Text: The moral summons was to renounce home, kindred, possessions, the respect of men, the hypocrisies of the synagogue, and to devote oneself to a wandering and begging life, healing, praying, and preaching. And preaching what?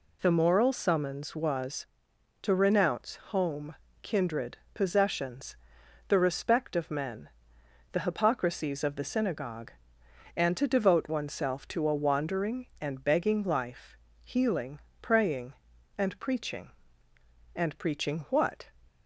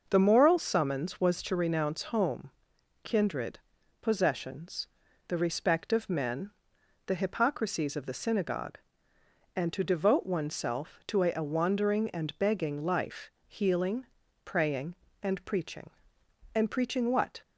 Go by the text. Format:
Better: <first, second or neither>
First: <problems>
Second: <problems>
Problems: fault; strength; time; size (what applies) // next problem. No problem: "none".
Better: first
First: none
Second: says "a" twice; at 11.3 s